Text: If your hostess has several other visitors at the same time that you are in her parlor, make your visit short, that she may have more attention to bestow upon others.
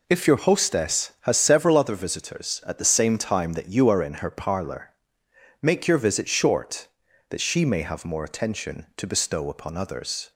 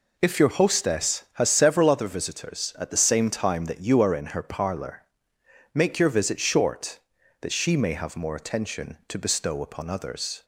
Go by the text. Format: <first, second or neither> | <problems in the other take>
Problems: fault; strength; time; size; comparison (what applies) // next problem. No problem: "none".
neither | none